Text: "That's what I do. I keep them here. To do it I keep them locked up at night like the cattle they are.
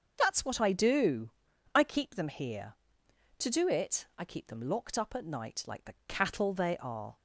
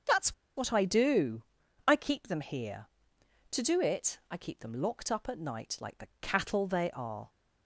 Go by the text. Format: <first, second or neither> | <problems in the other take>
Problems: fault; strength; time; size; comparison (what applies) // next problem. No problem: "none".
first | starts louder than the rest; until 1.2 s; 6.5 dB; also in the first // pauses between "That's" and "what"; slight; at 0.3 s; 0.22 s long